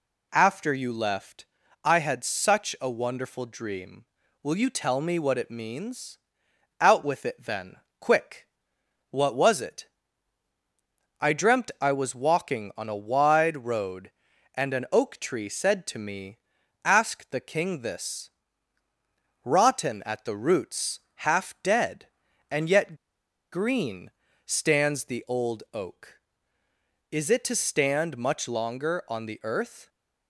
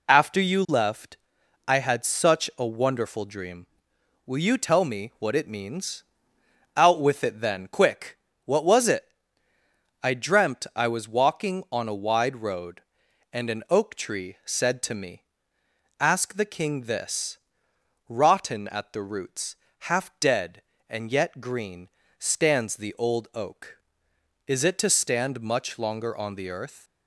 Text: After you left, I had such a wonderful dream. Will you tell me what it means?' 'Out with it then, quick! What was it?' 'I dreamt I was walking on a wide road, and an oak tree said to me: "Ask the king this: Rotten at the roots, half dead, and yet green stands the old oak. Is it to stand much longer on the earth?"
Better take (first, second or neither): second